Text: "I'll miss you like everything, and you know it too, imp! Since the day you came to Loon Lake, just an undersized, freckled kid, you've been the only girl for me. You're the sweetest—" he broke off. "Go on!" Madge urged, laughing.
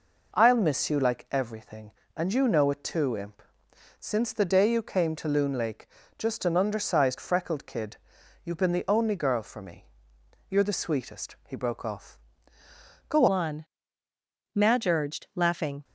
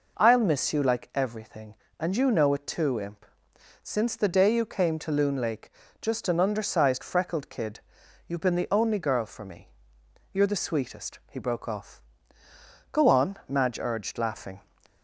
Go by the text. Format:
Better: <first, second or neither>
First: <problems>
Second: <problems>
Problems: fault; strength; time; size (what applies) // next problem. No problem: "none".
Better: second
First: changes voice at "on"; from 13.2 s on; 2.6 s long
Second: none